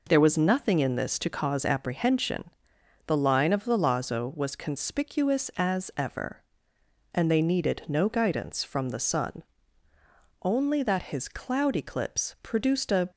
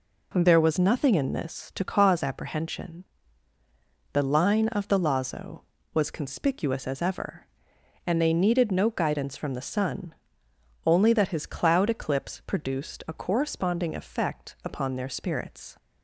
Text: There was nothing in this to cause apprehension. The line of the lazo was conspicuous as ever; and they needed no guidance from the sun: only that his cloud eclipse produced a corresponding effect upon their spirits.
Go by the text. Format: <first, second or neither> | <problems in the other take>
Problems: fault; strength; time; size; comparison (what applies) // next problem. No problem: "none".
second | stops before "corresponding effect upon their spirits"; at 13.1 s